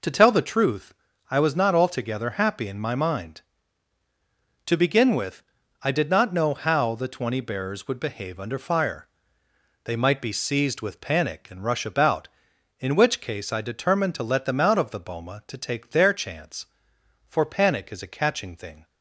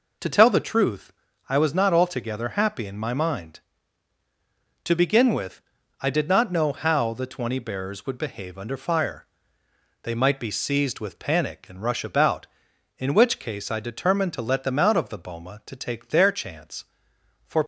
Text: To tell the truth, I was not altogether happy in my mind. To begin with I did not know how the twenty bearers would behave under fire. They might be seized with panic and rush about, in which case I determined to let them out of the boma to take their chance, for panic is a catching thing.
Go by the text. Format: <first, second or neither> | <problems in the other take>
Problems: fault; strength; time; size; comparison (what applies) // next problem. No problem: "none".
first | pauses between "with" and "I"; at 5.6 s; 0.38 s long; also in the first // stops before "panic is a catching thing"; at 17.6 s